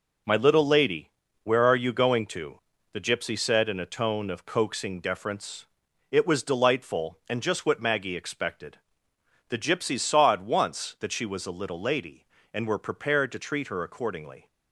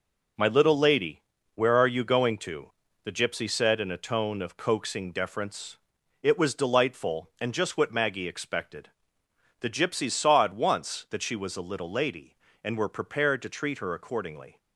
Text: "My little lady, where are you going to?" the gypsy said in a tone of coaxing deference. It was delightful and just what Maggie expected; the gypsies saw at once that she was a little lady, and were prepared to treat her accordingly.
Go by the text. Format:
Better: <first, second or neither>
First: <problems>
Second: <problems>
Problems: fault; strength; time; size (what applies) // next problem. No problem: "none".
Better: neither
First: none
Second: none